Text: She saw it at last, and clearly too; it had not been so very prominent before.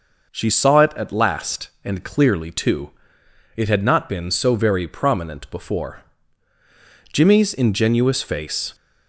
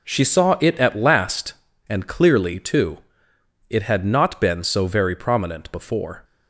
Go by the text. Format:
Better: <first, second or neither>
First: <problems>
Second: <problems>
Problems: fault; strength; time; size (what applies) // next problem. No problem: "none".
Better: second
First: goes on to say "Jimmy's ingenuous face"; from 7.1 s on; 1.6 s long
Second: none